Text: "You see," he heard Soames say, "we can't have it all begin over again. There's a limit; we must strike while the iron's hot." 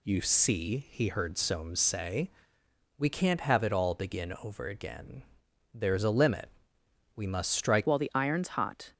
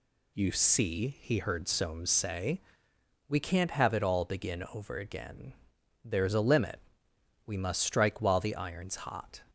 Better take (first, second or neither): second